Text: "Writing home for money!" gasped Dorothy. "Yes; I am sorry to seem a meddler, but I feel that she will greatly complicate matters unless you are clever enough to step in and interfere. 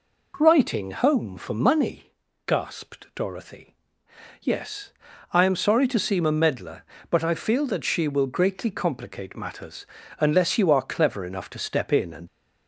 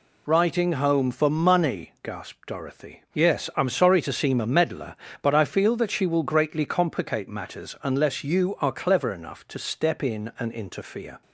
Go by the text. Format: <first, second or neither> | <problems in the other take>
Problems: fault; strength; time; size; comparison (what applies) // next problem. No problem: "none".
second | pauses between "matters" and "unless"; slight; at 9.8 s; 0.34 s long // stops before "interfere"; at 12.2 s